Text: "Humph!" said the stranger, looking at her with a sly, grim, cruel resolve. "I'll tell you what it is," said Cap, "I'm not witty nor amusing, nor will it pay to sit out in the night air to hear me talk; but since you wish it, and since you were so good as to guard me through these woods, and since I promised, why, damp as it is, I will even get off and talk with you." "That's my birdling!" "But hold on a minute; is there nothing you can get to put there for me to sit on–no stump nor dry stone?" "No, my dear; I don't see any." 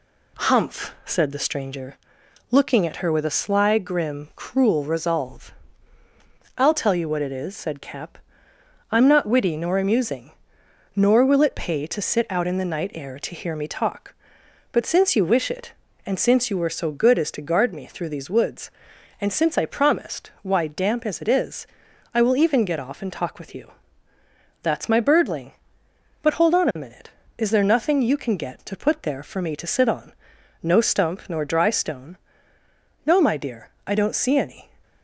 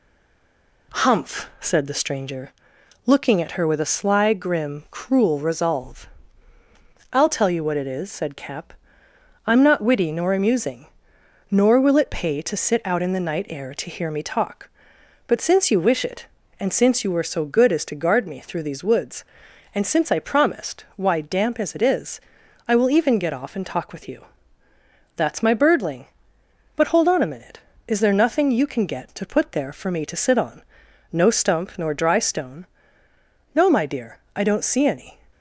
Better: first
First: none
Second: stays silent before the first word; slight; until 0.9 s; 0.9 s long

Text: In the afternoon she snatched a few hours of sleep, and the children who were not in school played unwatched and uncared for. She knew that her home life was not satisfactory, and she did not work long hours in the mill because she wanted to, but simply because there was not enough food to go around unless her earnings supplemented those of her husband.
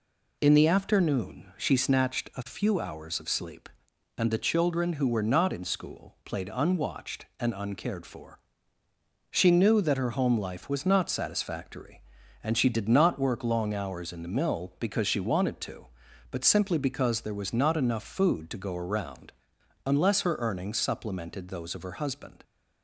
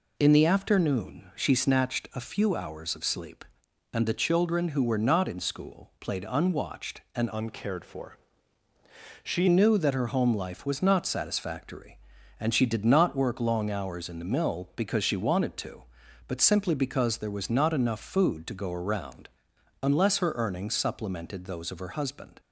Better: first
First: pauses between "around" and "unless"; noticeable; at 19.3 s; 0.52 s long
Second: changes voice from "uncared" to "She"; from 7.3 to 9.4 s; 2.1 s long // pauses between "around" and "unless"; noticeable; at 19.2 s; 0.52 s long

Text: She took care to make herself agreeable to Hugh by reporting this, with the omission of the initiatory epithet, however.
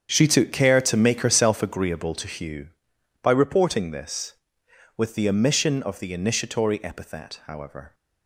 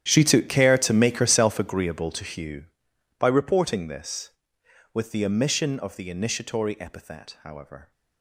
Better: first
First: starts louder than the rest; strong; until 1.1 s; 7.5 dB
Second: gets quieter; strong; throughout; 18 dB // starts louder than the rest; strong; until 1.0 s; 10.5 dB

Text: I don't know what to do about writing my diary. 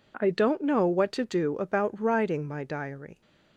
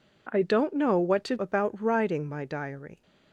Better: first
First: none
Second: skips "do"; at 1.3 s

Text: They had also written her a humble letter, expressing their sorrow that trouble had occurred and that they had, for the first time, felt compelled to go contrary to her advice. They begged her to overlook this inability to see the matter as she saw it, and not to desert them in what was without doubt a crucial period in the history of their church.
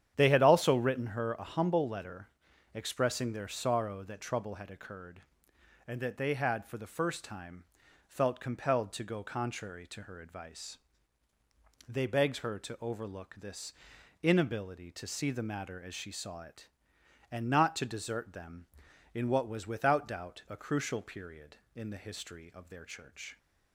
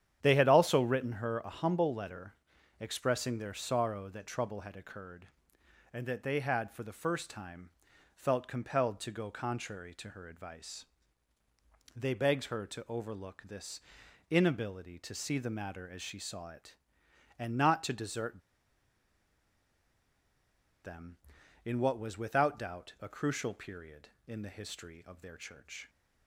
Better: first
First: starts louder than the rest; strong; until 1.1 s; 9.5 dB // pauses between "this" and "inability"; noticeable; at 13.7 s; 0.48 s long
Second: starts louder than the rest; strong; until 1.2 s; 9.5 dB // pauses between "this" and "inability"; noticeable; at 13.8 s; 0.48 s long // pauses between "desert" and "them"; strong; at 18.4 s; 2.4 s long

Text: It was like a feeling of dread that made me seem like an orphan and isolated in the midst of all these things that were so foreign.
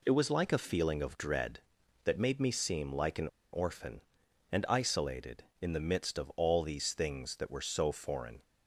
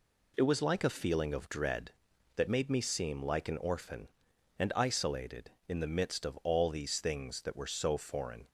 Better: second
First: pauses between "an" and "orphan"; slight; at 3.2 s; 0.25 s long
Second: none

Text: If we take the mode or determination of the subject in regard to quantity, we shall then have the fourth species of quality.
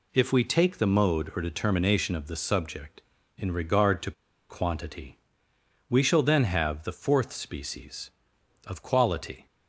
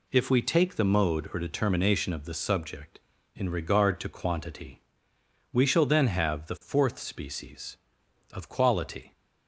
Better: second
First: pauses between "to" and "quantity"; at 4.1 s; 0.37 s long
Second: none

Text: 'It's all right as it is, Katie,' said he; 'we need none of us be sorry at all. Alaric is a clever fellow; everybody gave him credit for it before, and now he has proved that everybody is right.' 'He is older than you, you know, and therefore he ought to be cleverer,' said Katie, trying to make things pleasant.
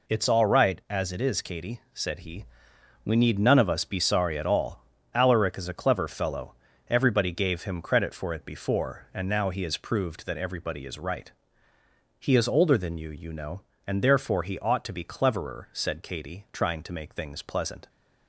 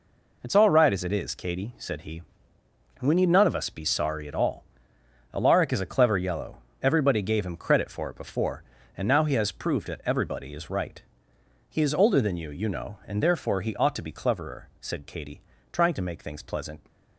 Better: first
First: none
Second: says "yellow" for "fellow"; at 6.1 s

